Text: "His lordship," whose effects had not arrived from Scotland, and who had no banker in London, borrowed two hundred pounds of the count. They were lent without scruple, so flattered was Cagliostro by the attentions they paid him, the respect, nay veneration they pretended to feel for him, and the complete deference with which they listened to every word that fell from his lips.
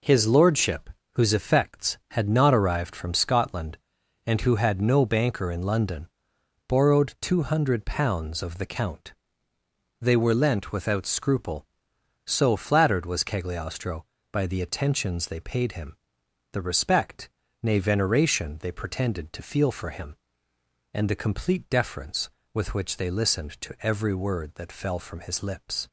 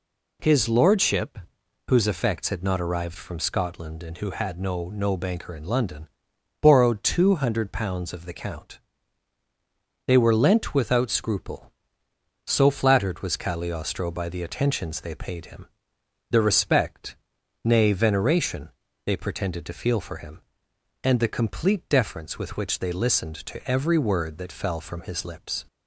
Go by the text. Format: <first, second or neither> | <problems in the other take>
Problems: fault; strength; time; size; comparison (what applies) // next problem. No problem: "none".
first | says "no" twice; at 4.8 s // pauses between "veneration" and "they"; slight; at 18.7 s; 0.34 s long